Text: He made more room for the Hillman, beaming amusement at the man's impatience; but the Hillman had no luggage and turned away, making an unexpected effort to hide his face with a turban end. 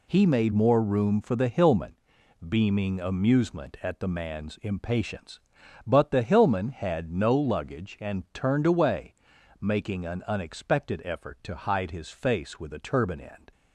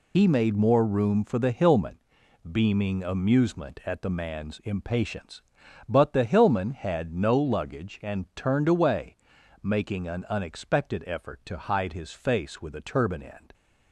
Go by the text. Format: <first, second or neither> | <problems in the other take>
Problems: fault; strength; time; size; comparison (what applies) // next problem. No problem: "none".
first | loses the start of "He"; at 0.1 s; 50 ms